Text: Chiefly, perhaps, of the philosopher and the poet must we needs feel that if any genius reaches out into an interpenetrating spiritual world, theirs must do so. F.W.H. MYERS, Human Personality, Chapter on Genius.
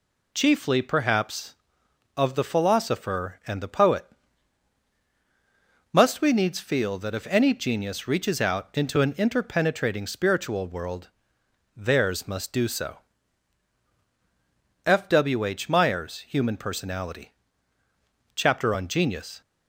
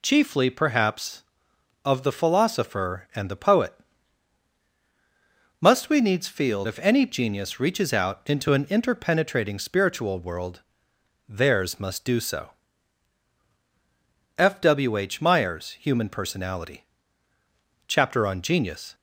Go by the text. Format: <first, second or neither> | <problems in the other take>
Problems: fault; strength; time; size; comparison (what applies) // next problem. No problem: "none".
first | pauses between "poet" and "must"; strong; at 3.7 s; 1.8 s long; strong in the first // skips "that"; at 6.6 s